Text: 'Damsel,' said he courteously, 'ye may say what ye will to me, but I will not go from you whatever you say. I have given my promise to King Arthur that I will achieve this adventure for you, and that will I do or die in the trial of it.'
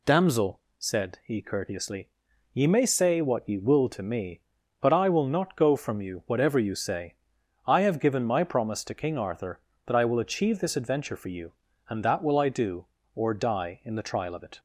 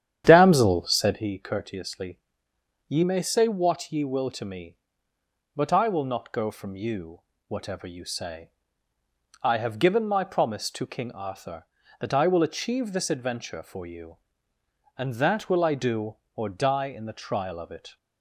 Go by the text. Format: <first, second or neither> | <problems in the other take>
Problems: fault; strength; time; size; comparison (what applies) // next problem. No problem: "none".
first | starts louder than the rest; strong; until 1.3 s; 10 dB // pauses between "you" and "whatever"; slight; at 7.2 s; 0.26 s long